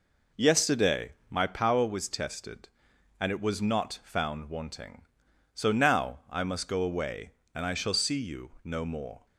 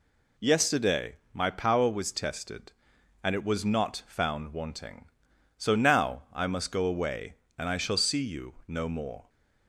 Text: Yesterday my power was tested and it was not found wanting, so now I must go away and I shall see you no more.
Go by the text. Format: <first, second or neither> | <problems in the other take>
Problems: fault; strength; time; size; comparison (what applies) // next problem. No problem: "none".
second | starts louder than the rest; noticeable; until 1.7 s; 4.5 dB // pauses between "Yesterday" and "my"; slight; at 1.1 s; 0.18 s long; slight in the second